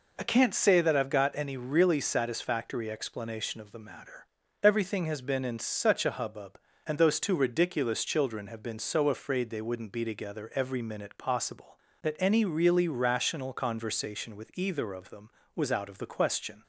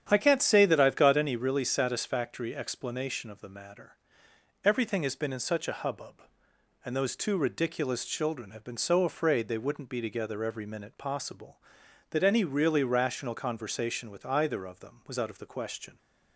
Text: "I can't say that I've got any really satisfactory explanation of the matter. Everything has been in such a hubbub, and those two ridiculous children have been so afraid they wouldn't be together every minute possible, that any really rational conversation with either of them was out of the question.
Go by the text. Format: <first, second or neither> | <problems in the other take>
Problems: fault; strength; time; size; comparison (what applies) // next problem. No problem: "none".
first | starts louder than the rest; strong; until 1.4 s; 9 dB